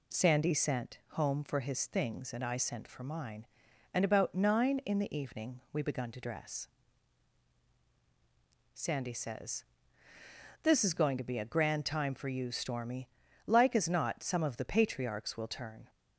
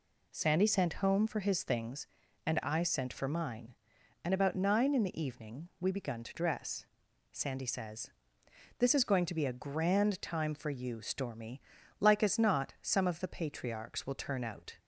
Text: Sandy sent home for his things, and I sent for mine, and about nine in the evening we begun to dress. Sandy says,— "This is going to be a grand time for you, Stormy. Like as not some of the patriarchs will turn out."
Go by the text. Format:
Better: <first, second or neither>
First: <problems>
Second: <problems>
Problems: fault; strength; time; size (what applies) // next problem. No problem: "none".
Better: second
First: stops before "out"; at 15.8 s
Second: none